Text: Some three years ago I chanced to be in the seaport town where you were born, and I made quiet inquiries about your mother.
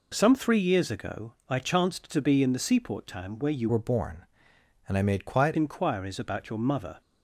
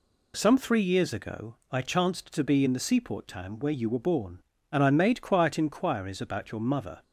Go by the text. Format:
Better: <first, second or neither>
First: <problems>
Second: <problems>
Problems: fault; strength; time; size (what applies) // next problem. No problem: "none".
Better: second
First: pauses between "ago" and "I"; slight; at 1.3 s; 0.16 s long // changes voice from "were" to "quiet"; from 3.6 to 5.5 s; 1.9 s long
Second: pauses between "ago" and "I"; slight; at 1.5 s; 0.16 s long